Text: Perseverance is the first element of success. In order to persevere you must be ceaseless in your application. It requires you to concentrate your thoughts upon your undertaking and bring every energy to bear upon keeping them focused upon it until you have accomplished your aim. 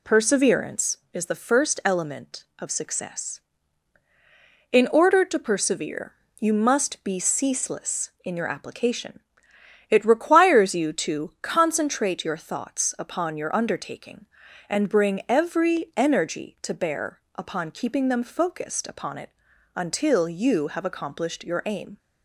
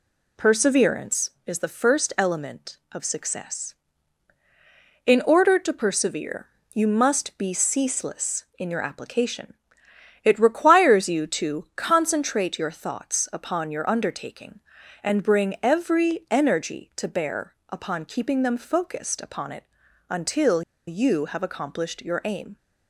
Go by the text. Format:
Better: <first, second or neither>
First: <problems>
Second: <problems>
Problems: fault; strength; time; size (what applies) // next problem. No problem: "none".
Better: first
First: pauses between "persevere" and "you"; slight; at 6.1 s; 0.26 s long // pauses between "bear" and "upon"; slight; at 17.1 s; 0.16 s long // pauses between "it" and "until"; noticeable; at 19.2 s; 0.46 s long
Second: pauses between "persevere" and "you"; slight; at 6.4 s; 0.26 s long // pauses between "bear" and "upon"; slight; at 17.5 s; 0.16 s long // pauses between "it" and "until"; noticeable; at 19.6 s; 0.46 s long // pauses between "until" and "you"; slight; at 20.6 s; 0.25 s long